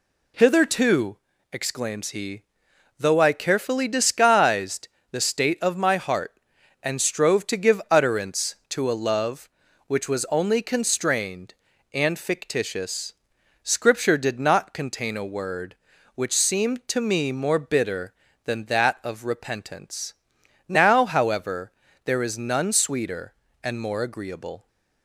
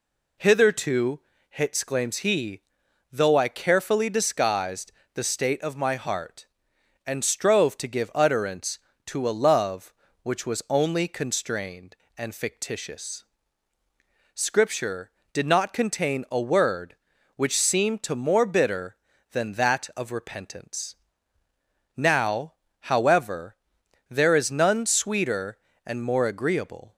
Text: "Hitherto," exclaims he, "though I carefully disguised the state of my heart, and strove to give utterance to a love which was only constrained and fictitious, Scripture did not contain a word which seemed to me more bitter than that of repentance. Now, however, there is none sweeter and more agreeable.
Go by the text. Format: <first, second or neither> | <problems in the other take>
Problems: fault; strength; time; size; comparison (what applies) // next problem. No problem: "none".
first | pauses between "disguised" and "the"; slight; at 4.9 s; 0.20 s long; slight in the first // skips "me"; at 18.1 s